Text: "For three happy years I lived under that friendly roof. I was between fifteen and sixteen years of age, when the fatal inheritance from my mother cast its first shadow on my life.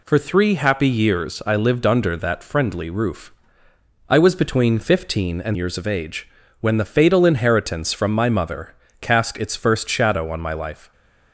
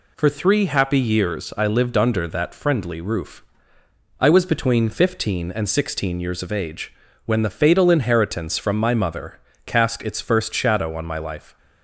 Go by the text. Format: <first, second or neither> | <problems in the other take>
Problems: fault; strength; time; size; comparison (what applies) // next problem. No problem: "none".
second | skips "sixteen"; at 5.5 s // pauses between "mother" and "cast"; slight; at 8.7 s; 0.24 s long; slight in the second